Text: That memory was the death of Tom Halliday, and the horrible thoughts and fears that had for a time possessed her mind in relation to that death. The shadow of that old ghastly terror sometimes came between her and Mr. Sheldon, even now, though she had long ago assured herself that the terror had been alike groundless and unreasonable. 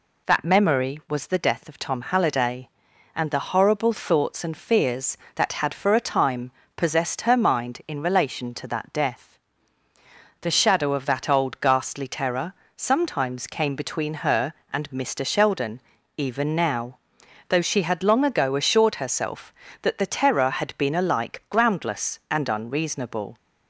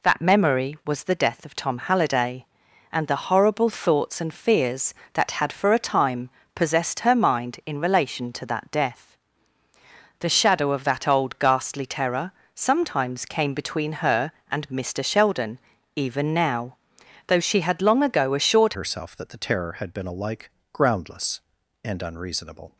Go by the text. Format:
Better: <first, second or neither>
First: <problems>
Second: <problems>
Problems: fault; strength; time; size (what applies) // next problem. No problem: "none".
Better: first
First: pauses between "time" and "possessed"; slight; at 6.5 s; 0.26 s long // pauses between "terror" and "sometimes"; slight; at 12.5 s; 0.22 s long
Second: pauses between "time" and "possessed"; slight; at 6.2 s; 0.26 s long // pauses between "terror" and "sometimes"; slight; at 12.3 s; 0.22 s long // changes voice at "herself"; from 18.7 s on; 4.0 s long // pauses between "alike" and "groundless"; slight; at 20.4 s; 0.24 s long